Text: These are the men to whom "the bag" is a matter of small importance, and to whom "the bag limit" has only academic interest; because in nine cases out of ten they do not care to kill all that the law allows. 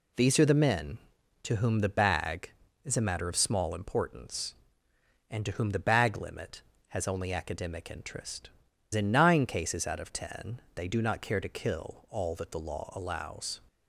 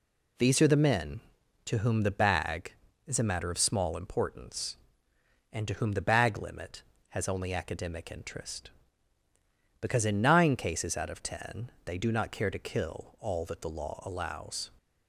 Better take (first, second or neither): second